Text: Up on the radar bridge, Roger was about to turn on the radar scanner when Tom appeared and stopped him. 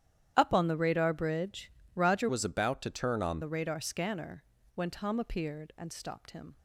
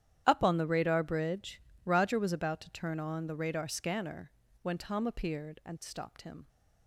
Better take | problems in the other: second | starts louder than the rest; strong; until 1.3 s; 10.5 dB; strong in the second // changes voice from "was" to "on"; from 2.2 to 3.3 s; 1.1 s long // pauses between "scanner" and "when"; slight; at 4.4 s; 0.32 s long; slight in the second

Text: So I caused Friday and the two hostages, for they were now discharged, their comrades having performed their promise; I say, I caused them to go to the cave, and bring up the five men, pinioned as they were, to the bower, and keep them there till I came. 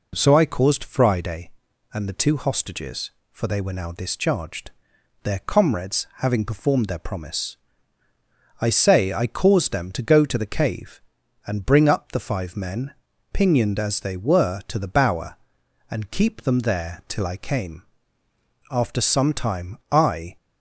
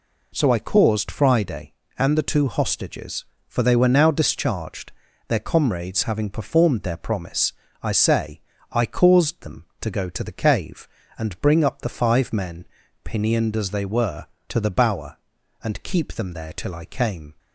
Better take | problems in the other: second | goes on to say "After some time I"; from 18.6 s on; 1.6 s long

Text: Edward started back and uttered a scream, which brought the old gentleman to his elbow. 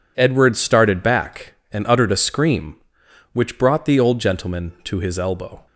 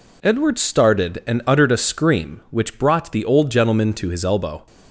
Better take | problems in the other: first | skips "back"; at 1.2 s

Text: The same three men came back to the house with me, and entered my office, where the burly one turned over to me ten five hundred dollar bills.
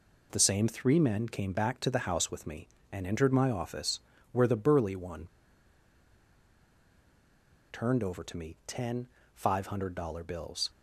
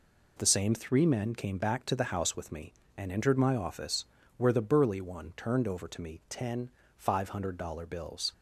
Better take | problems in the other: second | pauses between "one" and "turned"; strong; at 5.2 s; 2.4 s long // pauses between "ten" and "five"; slight; at 9.0 s; 0.26 s long; slight in the second

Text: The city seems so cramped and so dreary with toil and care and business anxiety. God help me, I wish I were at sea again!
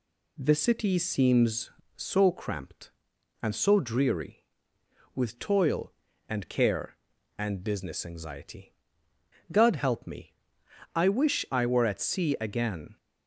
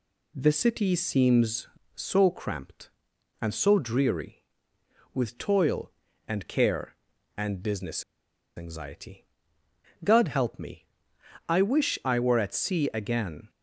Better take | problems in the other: first | pauses between "business" and "anxiety"; noticeable; at 8.0 s; 0.54 s long

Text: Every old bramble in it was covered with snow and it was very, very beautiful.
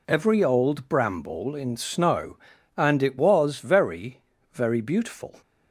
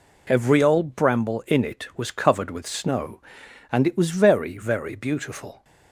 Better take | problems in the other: second | skips "it was covered with"; at 1.7 s

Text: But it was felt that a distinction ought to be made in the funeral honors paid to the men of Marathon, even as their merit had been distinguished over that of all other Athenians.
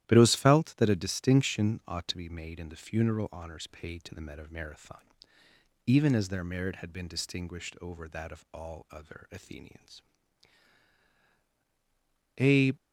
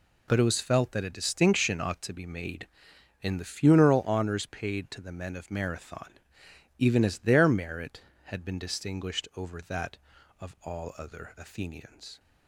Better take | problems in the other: second | starts louder than the rest; strong; until 1.0 s; 13 dB // goes on to say "A"; slight; from 12.3 s on; 0.34 s long

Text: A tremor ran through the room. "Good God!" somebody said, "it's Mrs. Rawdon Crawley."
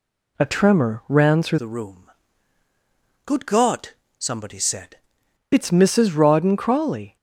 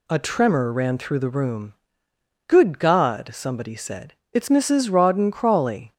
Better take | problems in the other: second | changes voice from "the" to "said"; from 1.5 to 4.9 s; 3.4 s long

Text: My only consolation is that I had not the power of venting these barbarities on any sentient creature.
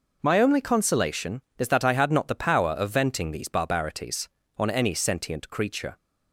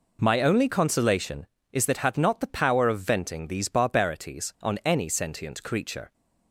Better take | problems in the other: first | skips "I"; at 2.0 s

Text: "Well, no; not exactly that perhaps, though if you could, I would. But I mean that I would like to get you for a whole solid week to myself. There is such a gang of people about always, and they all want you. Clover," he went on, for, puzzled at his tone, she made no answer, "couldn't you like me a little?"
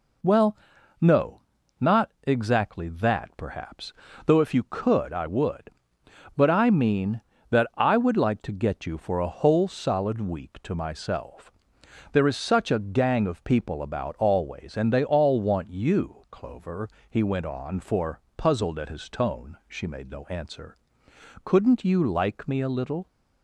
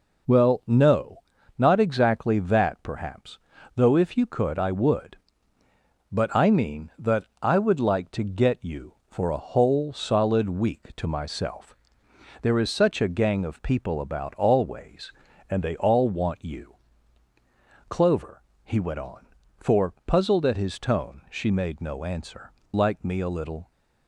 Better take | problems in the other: first | pauses between "that" and "I"; slight; at 7.2 s; 0.18 s long // skips "couldn't you"; at 22.6 s

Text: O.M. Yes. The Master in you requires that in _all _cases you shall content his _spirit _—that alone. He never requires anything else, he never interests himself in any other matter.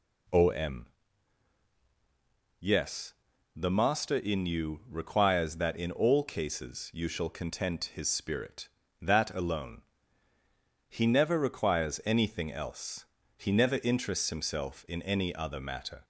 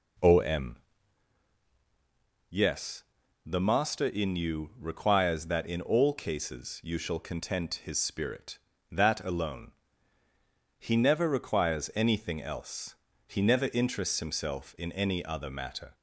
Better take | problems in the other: first | starts louder than the rest; until 1.3 s; 4 dB

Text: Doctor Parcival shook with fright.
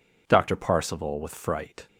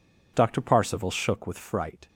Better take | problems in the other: second | skips "shook"; at 1.2 s

